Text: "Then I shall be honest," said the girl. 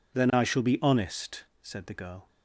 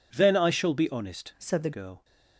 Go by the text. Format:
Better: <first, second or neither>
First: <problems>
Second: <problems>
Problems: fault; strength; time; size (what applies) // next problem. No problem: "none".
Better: first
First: none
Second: changes voice from "said" to "the"; from 1.3 to 1.7 s; 0.4 s long